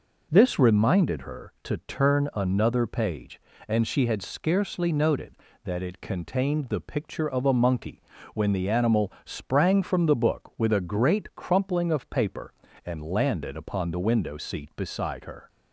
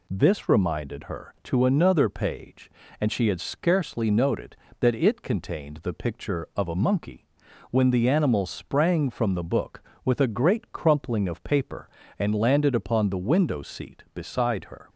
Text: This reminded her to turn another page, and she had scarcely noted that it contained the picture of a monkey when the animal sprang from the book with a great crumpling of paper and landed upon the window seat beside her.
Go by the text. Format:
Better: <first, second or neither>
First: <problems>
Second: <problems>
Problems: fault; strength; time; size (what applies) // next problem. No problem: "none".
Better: first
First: pauses between "monkey" and "when"; slight; at 8.0 s; 0.34 s long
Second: skips "turn"; at 1.6 s // pauses between "monkey" and "when"; noticeable; at 7.2 s; 0.46 s long